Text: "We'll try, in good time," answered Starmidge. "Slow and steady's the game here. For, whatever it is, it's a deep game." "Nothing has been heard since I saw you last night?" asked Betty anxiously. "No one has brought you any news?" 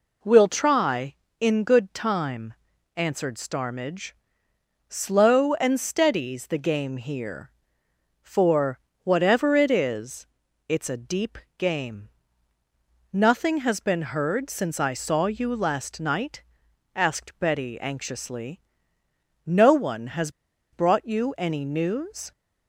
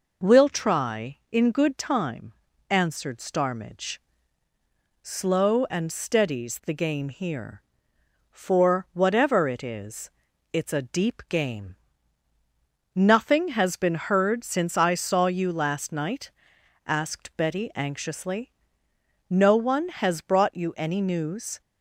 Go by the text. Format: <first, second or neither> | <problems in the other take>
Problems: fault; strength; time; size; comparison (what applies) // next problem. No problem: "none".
second | pauses between "deep" and "game"; slight; at 11.3 s; 0.18 s long // pauses between "has" and "brought"; at 20.3 s; 0.41 s long